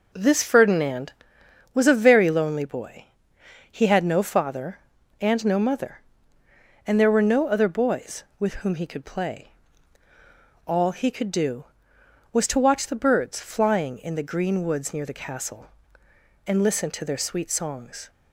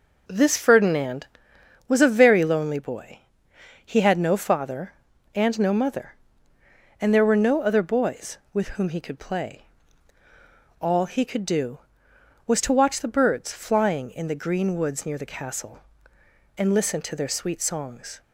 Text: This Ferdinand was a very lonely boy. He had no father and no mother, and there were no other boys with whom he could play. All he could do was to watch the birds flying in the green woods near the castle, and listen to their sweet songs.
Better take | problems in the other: neither | none

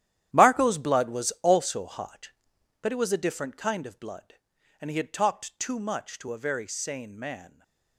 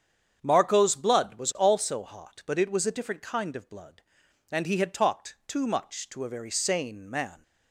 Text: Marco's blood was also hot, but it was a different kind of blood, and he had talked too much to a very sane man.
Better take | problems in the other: second | gets quieter; strong; throughout; 13.5 dB // starts louder than the rest; strong; until 1.3 s; 11.5 dB; strong in the second

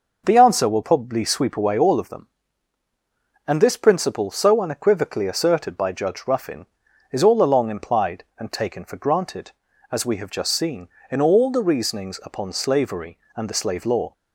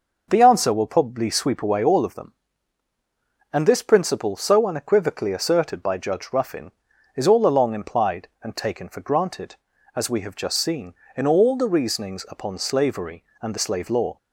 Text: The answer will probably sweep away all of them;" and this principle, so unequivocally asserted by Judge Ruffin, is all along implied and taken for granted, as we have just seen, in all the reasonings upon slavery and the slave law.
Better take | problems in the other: neither | none

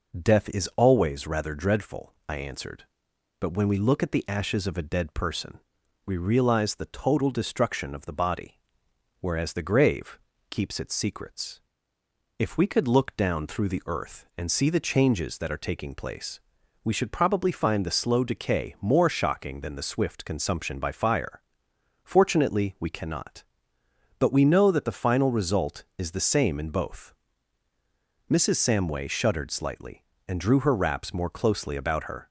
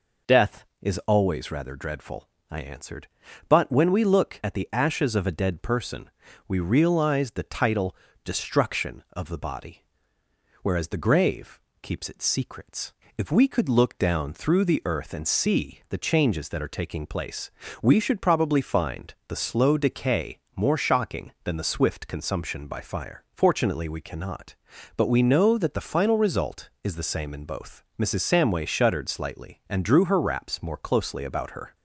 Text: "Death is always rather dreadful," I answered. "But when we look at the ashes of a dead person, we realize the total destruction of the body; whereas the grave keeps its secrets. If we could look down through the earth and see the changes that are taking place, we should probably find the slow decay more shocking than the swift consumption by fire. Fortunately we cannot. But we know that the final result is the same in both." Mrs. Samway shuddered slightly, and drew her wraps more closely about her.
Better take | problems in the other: first | says "title" for "total"; at 7.4 s // pauses between "grave" and "keeps"; slight; at 11.6 s; 0.22 s long; slight in the first // pauses between "decay" and "more"; slight; at 20.3 s; 0.18 s long

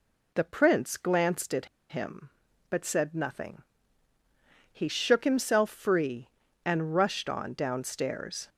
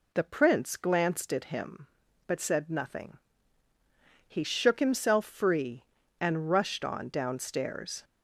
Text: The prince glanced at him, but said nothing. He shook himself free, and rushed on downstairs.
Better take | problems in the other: second | pauses between "at" and "him"; slight; at 1.6 s; 0.22 s long

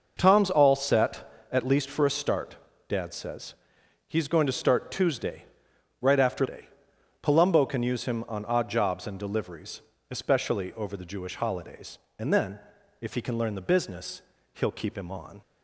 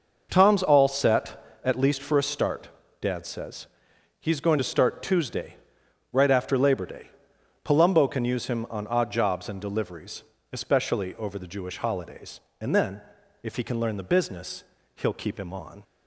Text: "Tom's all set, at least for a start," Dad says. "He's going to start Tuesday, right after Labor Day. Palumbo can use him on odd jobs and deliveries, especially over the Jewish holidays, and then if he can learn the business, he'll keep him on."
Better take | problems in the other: second | skips "Labor"; at 6.4 s // pauses between "then" and "if"; at 12.5 s; 0.42 s long; also in the second

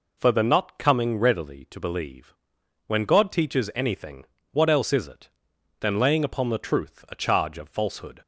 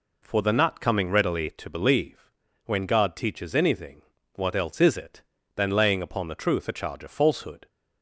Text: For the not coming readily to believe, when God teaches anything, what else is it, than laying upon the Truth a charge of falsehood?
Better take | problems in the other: neither | none

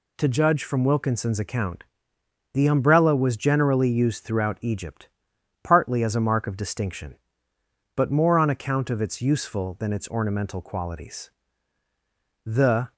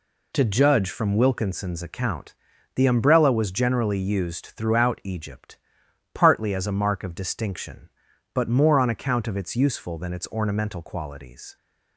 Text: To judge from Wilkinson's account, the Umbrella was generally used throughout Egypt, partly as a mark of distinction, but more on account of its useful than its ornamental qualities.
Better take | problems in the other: second | goes on to say "The"; slight; from 12.4 s on; 0.48 s long

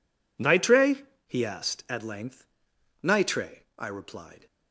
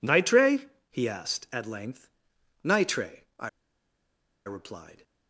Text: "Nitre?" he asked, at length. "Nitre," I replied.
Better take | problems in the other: first | pauses between "I" and "replied"; noticeable; at 3.4 s; 0.96 s long

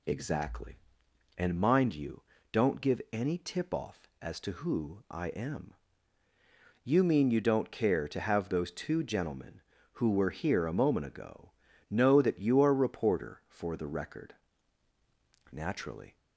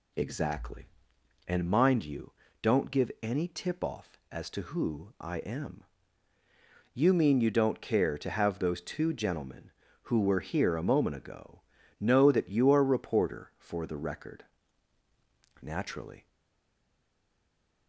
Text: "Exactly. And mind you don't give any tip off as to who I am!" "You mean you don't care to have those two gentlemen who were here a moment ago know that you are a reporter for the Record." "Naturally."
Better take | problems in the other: first | pauses between "you" and "don't"; slight; at 2.3 s; 0.28 s long; slight in the first // pauses between "ago" and "know"; slight; at 11.6 s; 0.36 s long; slight in the first // stays silent after the last word; noticeable; from 16.2 s on; 1.6 s long

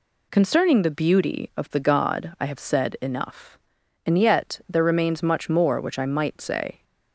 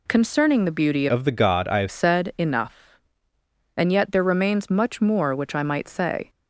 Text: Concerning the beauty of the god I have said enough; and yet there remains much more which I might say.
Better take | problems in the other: first | changes voice from "of" to "have"; from 1.0 to 1.8 s; 0.8 s long

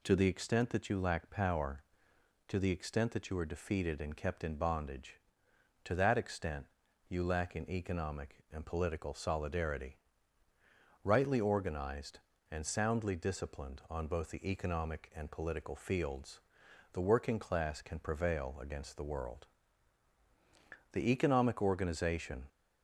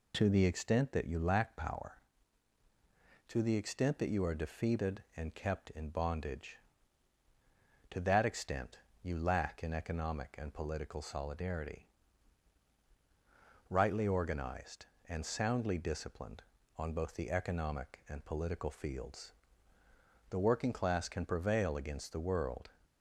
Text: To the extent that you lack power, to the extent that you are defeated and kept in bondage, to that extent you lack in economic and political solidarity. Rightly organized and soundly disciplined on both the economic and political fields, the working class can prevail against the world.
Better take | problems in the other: second | pauses between "extent" and "you"; at 6.6 s; 0.42 s long; slight in the second // goes on to say "The economic organization"; from 20.9 s on; 1.5 s long

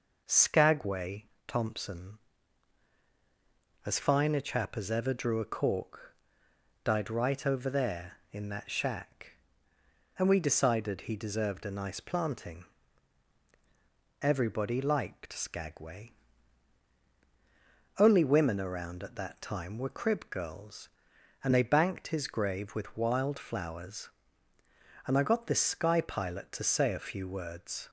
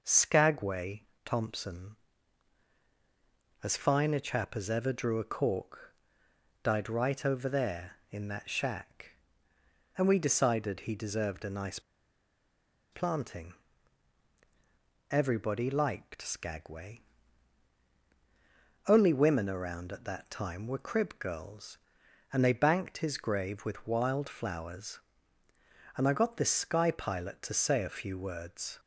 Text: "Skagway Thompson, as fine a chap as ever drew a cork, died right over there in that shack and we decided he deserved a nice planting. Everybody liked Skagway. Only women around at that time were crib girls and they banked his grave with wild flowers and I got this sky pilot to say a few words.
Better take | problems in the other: first | pauses between "Skagway" and "Thompson"; slight; at 1.0 s; 0.22 s long; slight in the first // pauses between "nice" and "planting"; at 11.7 s; 1.1 s long

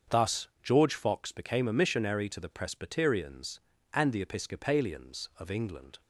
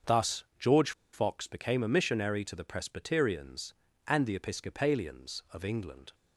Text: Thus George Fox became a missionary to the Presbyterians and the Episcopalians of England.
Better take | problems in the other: first | starts louder than the rest; until 1.4 s; 7 dB; also in the first // pauses between "Thus" and "George"; slight; at 0.4 s; 0.16 s long; slight in the first // pauses between "George" and "Fox"; slight; at 0.9 s; 0.22 s long

